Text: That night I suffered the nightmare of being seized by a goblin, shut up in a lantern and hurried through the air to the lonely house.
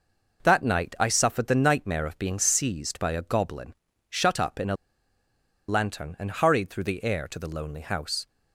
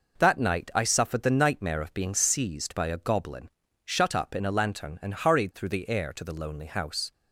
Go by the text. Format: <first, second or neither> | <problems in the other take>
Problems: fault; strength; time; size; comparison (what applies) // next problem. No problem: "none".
second | pauses between "a" and "lantern"; noticeable; at 4.7 s; 0.93 s long